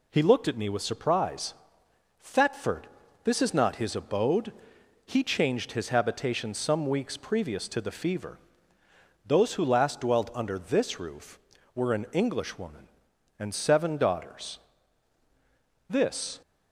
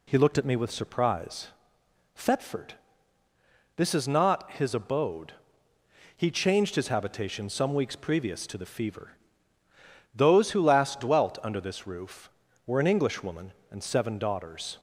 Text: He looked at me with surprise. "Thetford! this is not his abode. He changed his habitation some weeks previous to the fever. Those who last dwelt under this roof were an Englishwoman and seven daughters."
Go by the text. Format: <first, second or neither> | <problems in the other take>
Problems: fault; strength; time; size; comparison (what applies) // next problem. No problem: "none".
second | goes on to say "This"; from 15.8 s on; 0.52 s long